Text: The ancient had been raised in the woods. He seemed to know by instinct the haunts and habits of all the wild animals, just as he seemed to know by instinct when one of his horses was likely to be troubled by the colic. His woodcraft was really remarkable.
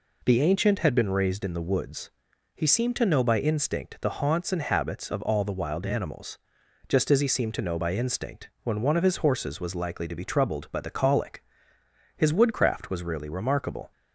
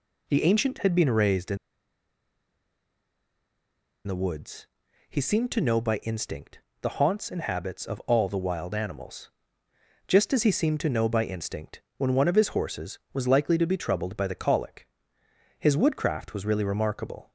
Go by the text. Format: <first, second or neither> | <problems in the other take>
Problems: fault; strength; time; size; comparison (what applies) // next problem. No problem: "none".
first | pauses between "in" and "the"; strong; at 1.5 s; 2.4 s long // pauses between "instinct" and "the"; slight; at 6.6 s; 0.20 s long // pauses between "instinct" and "when"; slight; at 11.8 s; 0.16 s long